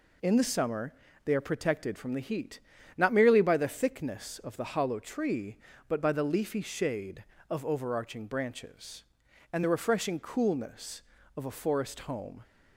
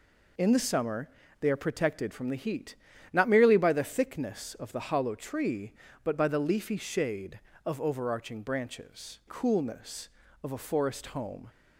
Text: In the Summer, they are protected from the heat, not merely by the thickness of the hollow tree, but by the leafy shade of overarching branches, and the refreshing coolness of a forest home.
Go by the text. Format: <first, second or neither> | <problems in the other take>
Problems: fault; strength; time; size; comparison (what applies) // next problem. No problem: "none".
first | skips "and the refreshing"; at 9.2 s